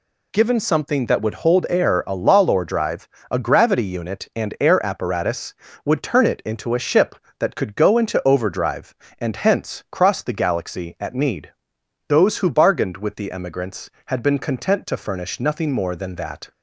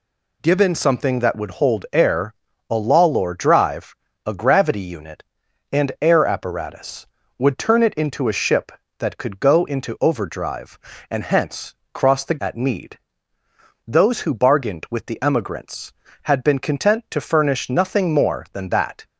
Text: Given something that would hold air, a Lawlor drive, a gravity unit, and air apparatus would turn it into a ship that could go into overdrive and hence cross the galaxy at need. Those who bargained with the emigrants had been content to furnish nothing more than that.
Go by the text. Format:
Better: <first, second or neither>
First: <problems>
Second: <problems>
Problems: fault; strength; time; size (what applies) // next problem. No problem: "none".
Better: first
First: none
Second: pauses between "hence" and "cross"; slight; at 11.7 s; 0.18 s long // skips "galaxy"; at 12.3 s